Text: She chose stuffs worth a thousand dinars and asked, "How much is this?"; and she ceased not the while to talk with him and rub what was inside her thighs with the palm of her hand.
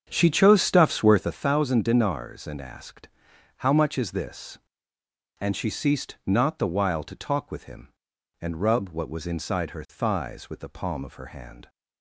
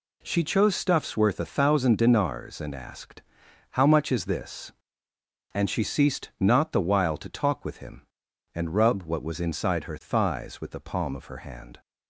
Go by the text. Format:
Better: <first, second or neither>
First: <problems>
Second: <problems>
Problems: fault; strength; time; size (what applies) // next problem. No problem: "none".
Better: second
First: starts louder than the rest; strong; until 1.4 s; 7.5 dB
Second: none